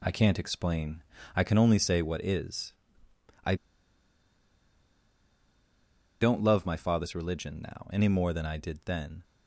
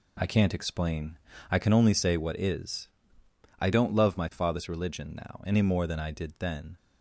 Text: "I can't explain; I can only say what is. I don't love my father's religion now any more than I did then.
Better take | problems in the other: second | pauses between "I" and "don't"; strong; at 3.5 s; 2.6 s long

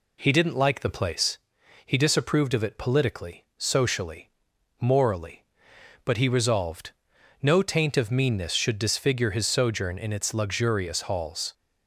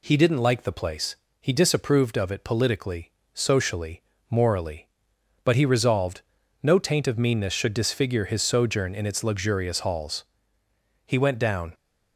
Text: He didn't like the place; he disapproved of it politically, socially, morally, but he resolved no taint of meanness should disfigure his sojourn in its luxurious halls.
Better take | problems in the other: first | pauses between "resolved" and "no"; at 6.2 s; 0.42 s long; noticeable in the first // goes on to say "He went down"; noticeable; from 11.0 s on; 0.66 s long

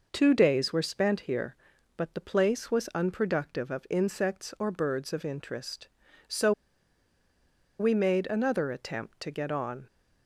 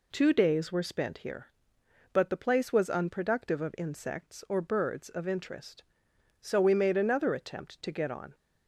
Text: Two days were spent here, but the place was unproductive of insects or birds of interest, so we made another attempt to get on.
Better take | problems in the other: second | pauses between "so" and "we"; strong; at 6.5 s; 1.2 s long

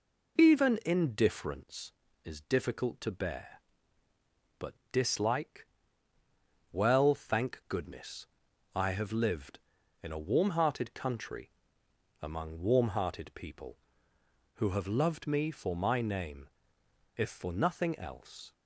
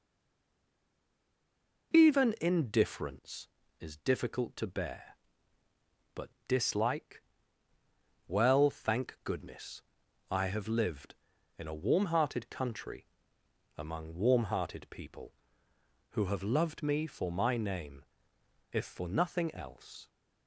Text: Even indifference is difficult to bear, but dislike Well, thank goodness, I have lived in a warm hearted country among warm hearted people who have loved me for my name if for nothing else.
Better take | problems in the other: first | stays silent before the first word; noticeable; until 1.9 s; 1.9 s long // pauses between "but" and "dislike"; slight; at 6.3 s; 0.18 s long; slight in the first // pauses between "dislike" and "Well"; at 7.2 s; 1.0 s long; also in the first // pauses between "country" and "among"; noticeable; at 13.0 s; 0.72 s long; noticeable in the first // pauses between "name" and "if"; noticeable; at 18.0 s; 0.66 s long; noticeable in the first

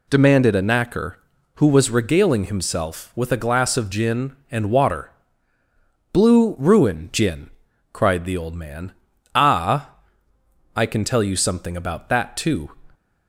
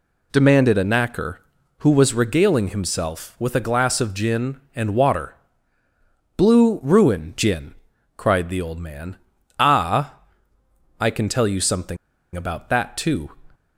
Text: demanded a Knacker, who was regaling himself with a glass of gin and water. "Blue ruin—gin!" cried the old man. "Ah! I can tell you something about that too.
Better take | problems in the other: first | pauses between "something" and "about"; at 11.9 s; 0.38 s long

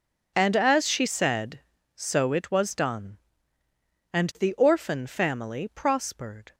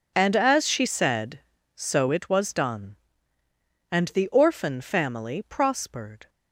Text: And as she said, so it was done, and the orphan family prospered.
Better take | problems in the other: neither | none

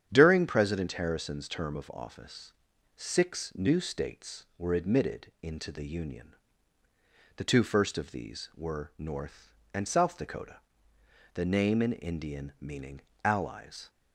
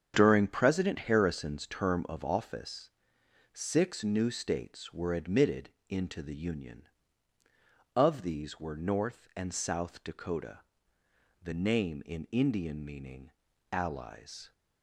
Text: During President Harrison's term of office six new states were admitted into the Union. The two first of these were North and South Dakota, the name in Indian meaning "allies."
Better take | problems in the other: first | starts louder than the rest; strong; until 1.2 s; 8.5 dB; strong in the first // pauses between "office" and "six"; noticeable; at 2.8 s; 0.64 s long; also in the first // pauses between "admitted" and "into"; slight; at 5.7 s; 0.18 s long; slight in the first // skips "The two first"; at 7.4 s // pauses between "meaning" and "allies"; at 13.3 s; 0.40 s long; slight in the first

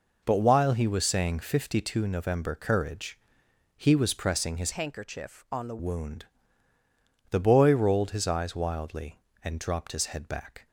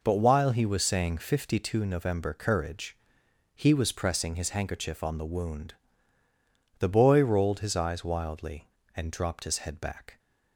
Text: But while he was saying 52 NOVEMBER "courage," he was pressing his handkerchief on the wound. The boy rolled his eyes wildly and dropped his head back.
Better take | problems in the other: second | changes voice from "handkerchief" to "the"; from 4.7 to 5.7 s; 1.0 s long

